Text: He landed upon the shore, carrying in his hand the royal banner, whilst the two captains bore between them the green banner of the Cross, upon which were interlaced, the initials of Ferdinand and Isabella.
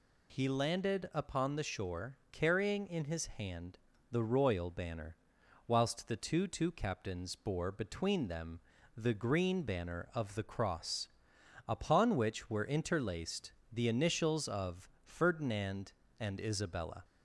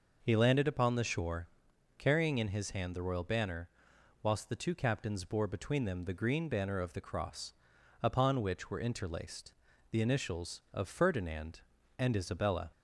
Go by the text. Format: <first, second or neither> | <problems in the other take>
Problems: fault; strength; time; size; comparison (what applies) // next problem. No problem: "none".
second | pauses between "hand" and "the"; slight; at 3.7 s; 0.32 s long // says "two" twice; at 6.4 s // pauses between "them" and "the"; slight; at 8.6 s; 0.34 s long